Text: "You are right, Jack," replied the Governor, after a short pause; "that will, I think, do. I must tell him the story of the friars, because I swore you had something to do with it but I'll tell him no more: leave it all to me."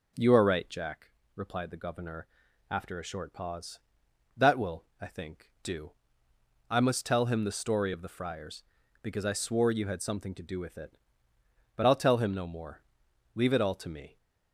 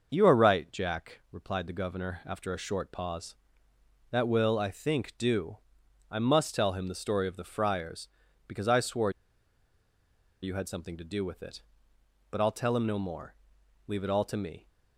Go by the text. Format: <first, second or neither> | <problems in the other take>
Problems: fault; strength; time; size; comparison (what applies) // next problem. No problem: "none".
first | starts louder than the rest; noticeable; until 1.1 s; 6 dB // pauses between "swore" and "you"; strong; at 9.0 s; 1.3 s long